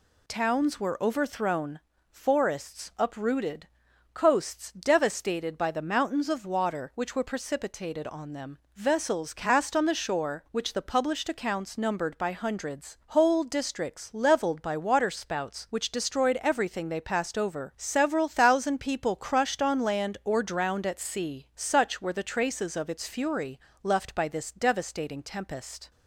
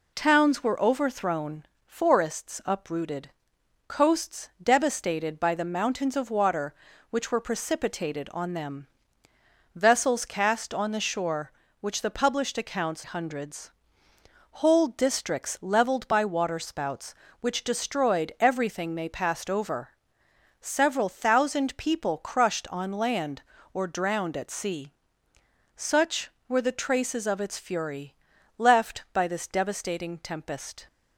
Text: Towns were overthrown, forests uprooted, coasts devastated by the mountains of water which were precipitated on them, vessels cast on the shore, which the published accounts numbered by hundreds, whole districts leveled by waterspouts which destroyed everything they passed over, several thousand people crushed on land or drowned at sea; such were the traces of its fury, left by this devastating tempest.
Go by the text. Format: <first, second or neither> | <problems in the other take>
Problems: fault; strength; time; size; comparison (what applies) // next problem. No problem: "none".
first | skips "numbered by"; at 13.0 s